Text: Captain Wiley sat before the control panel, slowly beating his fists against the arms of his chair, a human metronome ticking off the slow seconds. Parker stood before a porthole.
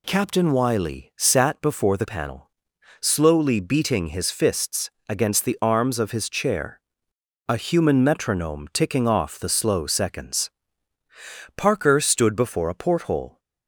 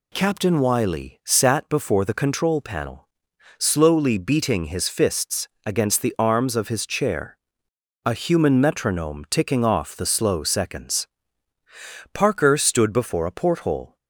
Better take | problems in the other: second | skips "control"; at 2.0 s // pauses between "fists" and "against"; slight; at 4.8 s; 0.18 s long; slight in the second

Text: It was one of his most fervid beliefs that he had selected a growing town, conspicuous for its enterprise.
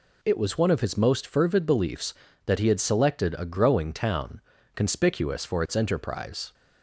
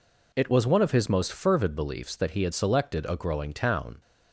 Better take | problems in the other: first | stops before "conspicuous for its enterprise"; at 4.0 s

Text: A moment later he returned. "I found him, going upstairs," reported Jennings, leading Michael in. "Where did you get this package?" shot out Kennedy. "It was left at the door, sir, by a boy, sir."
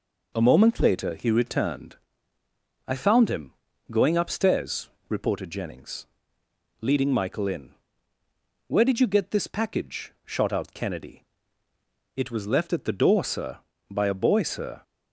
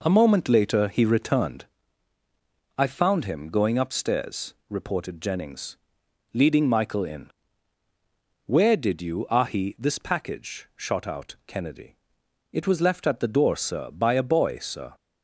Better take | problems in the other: first | says "ahi" for "get"; at 9.2 s

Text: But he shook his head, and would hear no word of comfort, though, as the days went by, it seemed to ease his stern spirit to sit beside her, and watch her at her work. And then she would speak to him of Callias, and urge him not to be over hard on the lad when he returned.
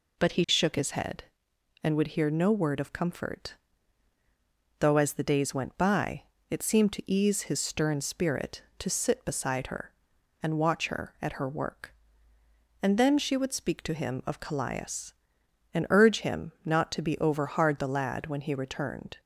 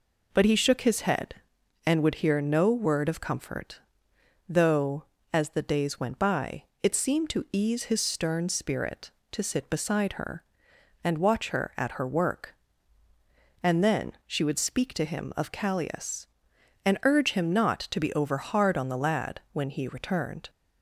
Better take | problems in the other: second | skips "on"; at 17.7 s

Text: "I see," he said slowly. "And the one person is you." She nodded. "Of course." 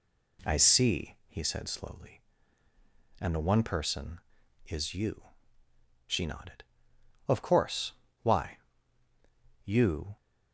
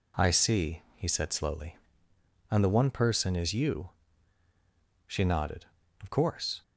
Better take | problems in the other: second | goes on to say "Why You"; strong; from 8.2 s on; 1.9 s long

